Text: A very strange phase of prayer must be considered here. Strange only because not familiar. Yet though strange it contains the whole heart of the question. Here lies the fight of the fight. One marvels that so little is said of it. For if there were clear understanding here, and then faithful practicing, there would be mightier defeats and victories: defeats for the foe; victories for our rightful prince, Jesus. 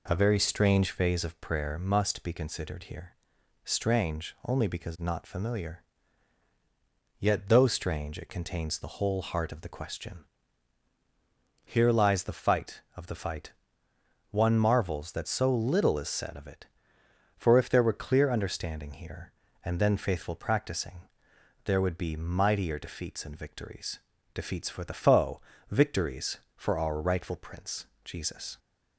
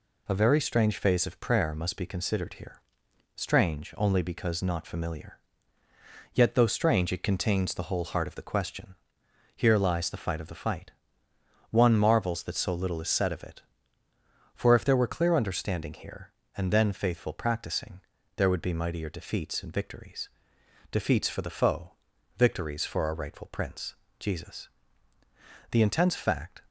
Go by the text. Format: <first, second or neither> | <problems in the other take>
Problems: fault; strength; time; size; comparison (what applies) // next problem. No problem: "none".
first | goes on to say "The intense fact"; noticeable; from 25.7 s on; 0.90 s long